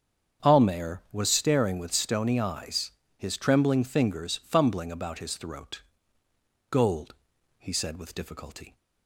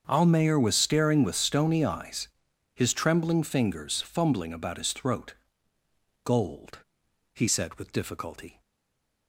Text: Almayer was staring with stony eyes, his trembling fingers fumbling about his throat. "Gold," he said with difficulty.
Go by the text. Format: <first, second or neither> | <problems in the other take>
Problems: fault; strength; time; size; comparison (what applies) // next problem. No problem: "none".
first | starts louder than the rest; until 1.0 s; 6.5 dB; strong in the first // stays silent after the last word; slight; from 8.6 s on; 0.6 s long